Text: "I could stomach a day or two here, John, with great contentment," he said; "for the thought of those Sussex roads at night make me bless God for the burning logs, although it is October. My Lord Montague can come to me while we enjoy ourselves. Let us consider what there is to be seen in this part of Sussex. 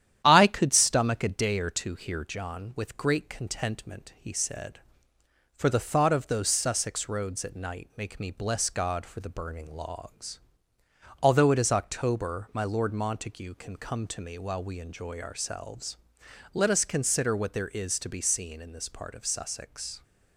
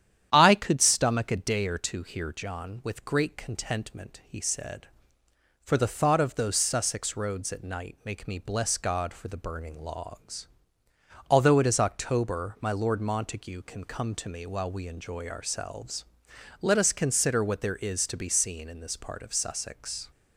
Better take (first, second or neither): second